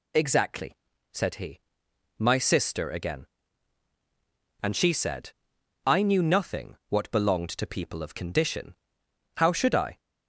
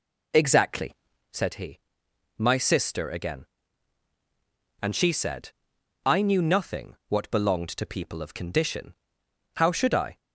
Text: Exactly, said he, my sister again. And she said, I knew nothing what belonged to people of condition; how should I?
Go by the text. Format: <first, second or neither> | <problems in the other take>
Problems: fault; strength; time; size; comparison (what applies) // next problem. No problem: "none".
first | starts louder than the rest; until 1.4 s; 3.5 dB